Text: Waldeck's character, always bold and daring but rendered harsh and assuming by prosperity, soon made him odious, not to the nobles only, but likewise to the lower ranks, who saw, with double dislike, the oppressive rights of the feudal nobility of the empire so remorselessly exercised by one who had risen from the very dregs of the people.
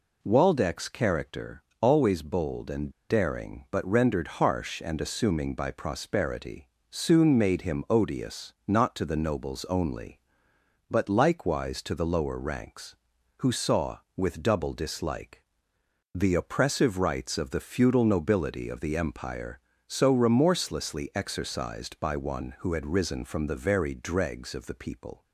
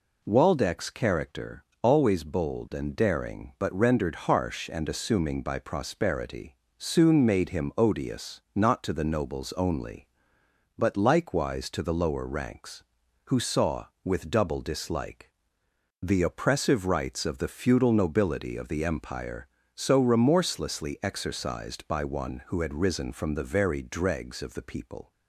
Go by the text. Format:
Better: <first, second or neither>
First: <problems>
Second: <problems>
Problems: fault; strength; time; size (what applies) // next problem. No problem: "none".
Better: second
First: pauses between "and" and "daring"; slight; at 2.9 s; 0.18 s long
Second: none